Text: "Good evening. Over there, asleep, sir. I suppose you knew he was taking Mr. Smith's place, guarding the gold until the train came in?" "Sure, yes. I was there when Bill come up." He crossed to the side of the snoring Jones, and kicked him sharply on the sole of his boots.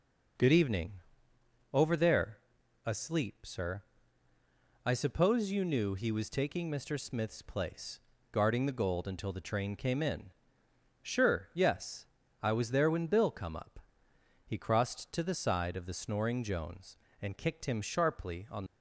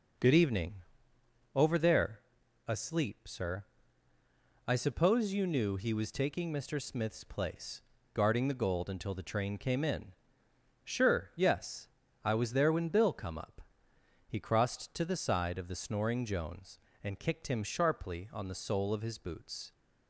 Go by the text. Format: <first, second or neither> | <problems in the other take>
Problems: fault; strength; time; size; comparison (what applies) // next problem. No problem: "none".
second | stops before "the sole of his boots"; at 18.6 s